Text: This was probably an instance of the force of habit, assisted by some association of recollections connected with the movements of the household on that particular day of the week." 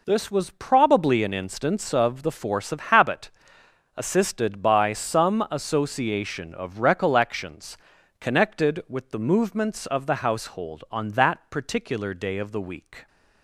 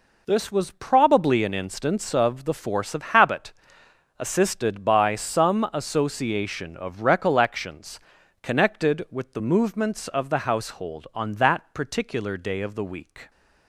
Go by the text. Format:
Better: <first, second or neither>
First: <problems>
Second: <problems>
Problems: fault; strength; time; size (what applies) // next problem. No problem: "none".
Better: neither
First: pauses between "recollections" and "connected"; at 7.7 s; 0.44 s long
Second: pauses between "recollections" and "connected"; at 7.9 s; 0.44 s long